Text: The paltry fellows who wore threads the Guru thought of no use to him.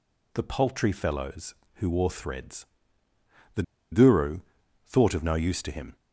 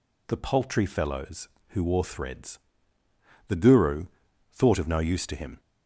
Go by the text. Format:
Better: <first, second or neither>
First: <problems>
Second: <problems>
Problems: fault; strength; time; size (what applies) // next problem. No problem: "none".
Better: second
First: pauses between "threads" and "the"; noticeable; at 2.6 s; 0.90 s long // pauses between "the" and "Guru"; slight; at 3.6 s; 0.29 s long // pauses between "Guru" and "thought"; at 4.4 s; 0.44 s long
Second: pauses between "threads" and "the"; noticeable; at 2.5 s; 0.90 s long // pauses between "Guru" and "thought"; at 4.0 s; 0.44 s long